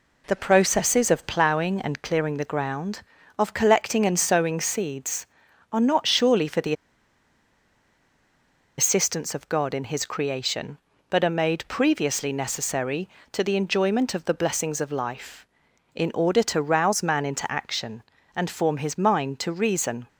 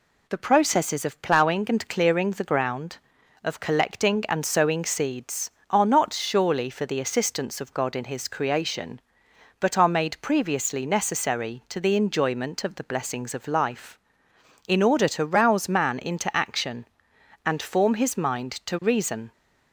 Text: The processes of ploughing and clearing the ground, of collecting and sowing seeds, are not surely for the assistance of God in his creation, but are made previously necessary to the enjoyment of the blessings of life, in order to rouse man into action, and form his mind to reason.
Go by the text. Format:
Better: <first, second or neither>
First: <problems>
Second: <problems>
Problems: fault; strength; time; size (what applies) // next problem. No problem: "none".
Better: second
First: pauses between "the" and "assistance"; strong; at 6.7 s; 2.0 s long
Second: none